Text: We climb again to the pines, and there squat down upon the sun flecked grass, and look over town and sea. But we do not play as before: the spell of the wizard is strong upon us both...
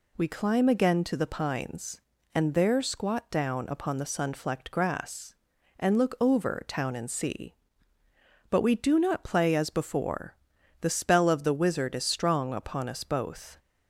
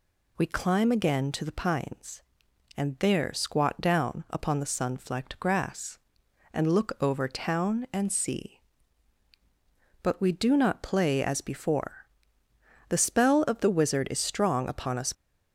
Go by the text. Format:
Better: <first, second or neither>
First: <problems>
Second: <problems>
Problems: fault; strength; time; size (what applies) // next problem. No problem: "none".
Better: first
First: none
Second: stops before "both"; at 15.1 s